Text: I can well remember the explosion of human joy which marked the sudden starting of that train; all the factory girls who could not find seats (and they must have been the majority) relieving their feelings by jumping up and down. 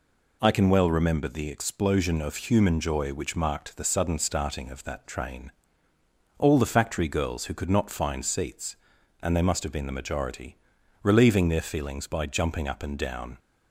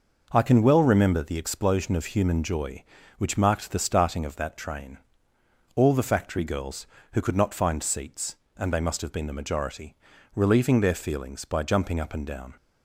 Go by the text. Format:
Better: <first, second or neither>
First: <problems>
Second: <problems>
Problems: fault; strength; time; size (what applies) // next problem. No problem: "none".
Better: first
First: none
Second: skips "sudden"; at 3.7 s